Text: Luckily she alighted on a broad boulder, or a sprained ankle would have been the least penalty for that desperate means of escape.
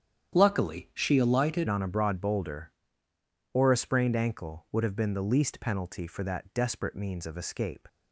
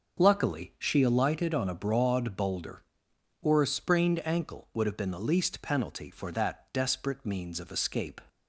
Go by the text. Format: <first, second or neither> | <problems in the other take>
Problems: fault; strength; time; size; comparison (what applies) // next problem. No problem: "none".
second | starts louder than the rest; strong; until 1.4 s; 9.5 dB; noticeable in the second // changes voice at "on"; from 1.6 s on; 6.2 s long